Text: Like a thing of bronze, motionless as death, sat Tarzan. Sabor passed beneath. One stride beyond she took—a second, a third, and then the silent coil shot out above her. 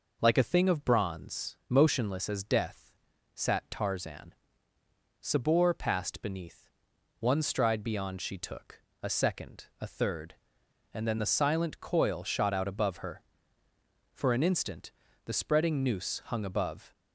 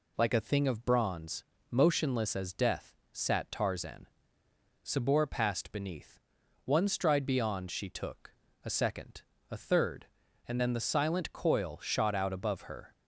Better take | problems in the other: second | goes on to say "For an instant the spreading noose hung above"; strong; from 14.1 s on; 2.8 s long

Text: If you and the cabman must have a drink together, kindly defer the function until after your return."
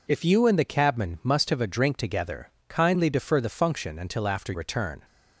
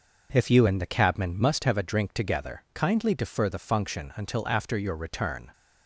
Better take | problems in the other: second | skips "your"; at 4.5 s

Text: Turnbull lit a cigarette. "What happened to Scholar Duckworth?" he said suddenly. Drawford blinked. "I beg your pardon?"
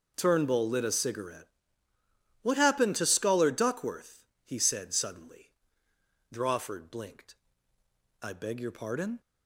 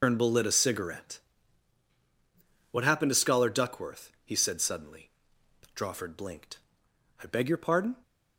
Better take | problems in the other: first | loses the start of "Turnbull"; at 0.0 s; 130 ms

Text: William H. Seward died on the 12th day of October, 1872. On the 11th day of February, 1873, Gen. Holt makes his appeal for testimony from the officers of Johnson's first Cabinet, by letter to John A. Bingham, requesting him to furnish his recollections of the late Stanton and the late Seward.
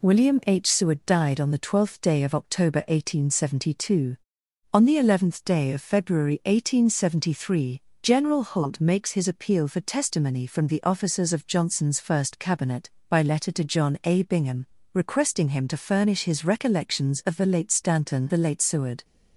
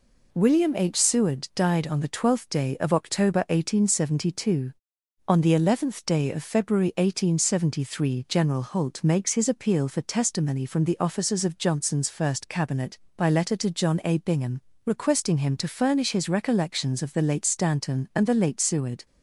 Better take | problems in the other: second | skips "and"; at 18.3 s

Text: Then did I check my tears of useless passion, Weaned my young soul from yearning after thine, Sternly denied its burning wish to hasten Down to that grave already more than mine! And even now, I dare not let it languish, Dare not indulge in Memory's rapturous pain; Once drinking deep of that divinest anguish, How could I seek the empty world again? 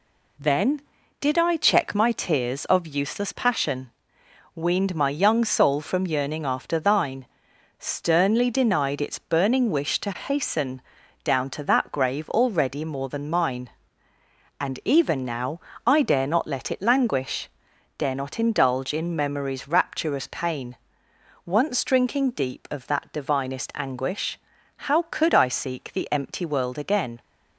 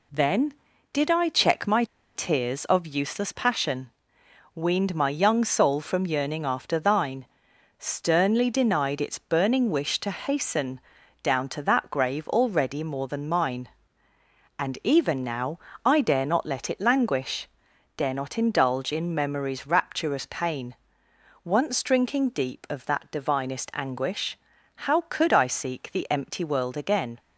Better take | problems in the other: first | pauses between "my" and "tears"; slight; at 1.8 s; 0.30 s long // pauses between "hasten" and "Down"; at 10.7 s; 0.44 s long; also in the first

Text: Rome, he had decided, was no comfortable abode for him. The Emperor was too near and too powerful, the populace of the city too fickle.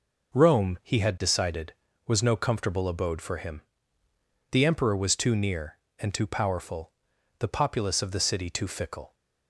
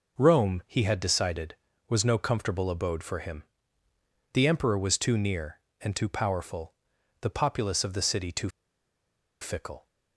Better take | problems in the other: first | pauses between "too" and "fickle"; noticeable; at 8.4 s; 0.91 s long

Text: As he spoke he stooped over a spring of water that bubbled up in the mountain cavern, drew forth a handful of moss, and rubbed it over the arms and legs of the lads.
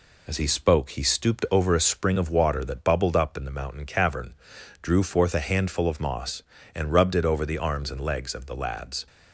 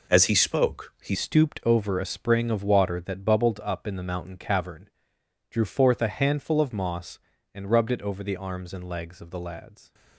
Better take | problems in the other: first | changes voice at "stooped"; from 1.1 s on; 8.8 s long

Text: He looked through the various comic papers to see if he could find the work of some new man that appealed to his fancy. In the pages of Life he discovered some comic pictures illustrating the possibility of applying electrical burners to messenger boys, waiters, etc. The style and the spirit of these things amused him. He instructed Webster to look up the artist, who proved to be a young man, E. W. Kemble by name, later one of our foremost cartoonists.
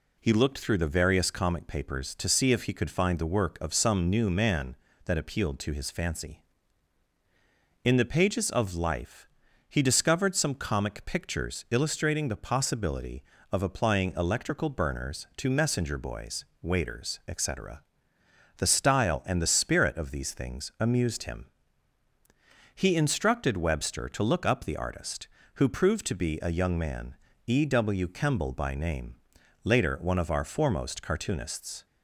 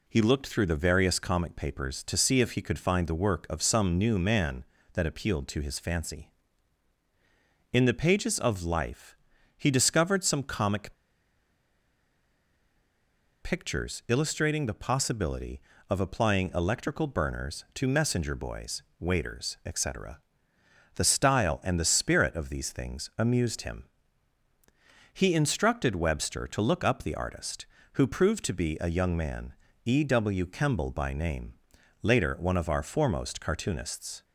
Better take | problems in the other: first | pauses between "Life" and "he"; at 9.1 s; 0.42 s long; also in the first // pauses between "comic" and "pictures"; strong; at 10.9 s; 2.4 s long

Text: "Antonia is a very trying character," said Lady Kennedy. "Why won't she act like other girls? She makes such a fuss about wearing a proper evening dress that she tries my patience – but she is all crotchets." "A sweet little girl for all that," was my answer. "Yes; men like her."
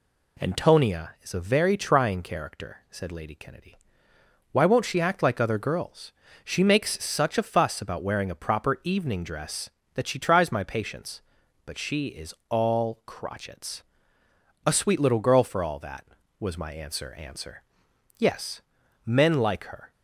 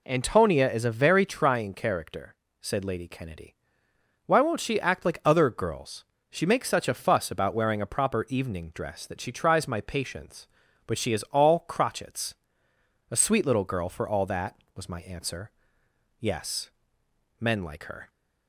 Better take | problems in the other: second | says "answer" twice; at 17.1 s

